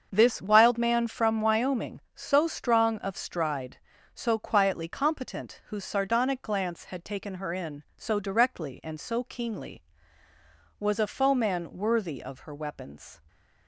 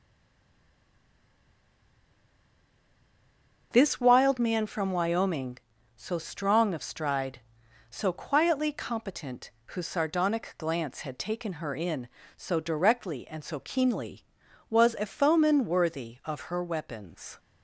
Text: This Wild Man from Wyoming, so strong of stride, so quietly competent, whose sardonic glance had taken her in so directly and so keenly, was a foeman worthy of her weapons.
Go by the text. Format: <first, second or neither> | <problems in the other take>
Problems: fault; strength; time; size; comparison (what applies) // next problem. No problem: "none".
first | stays silent before the first word; strong; until 3.7 s; 3.7 s long // starts louder than the rest; until 4.7 s; 6 dB; also in the first